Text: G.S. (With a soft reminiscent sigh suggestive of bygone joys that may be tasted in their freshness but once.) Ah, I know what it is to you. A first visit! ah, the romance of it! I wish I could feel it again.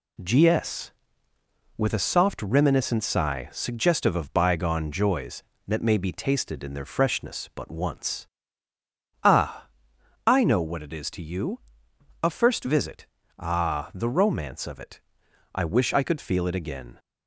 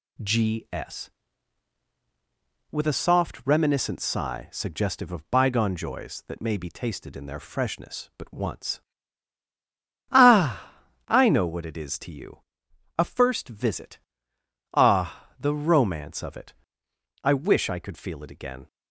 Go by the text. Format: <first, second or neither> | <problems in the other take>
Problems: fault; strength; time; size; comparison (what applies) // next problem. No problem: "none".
neither | none